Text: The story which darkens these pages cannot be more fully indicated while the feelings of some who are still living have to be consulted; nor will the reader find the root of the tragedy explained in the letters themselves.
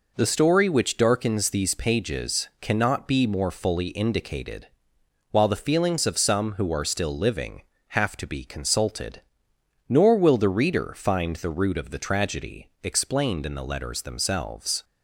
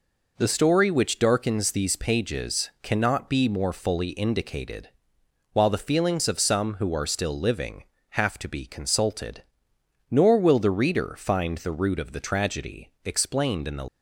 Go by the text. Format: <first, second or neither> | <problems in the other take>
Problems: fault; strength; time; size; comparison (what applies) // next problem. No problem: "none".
first | pauses between "indicated" and "while"; noticeable; at 4.8 s; 0.64 s long; noticeable in the first // stops before "letters themselves"; at 13.8 s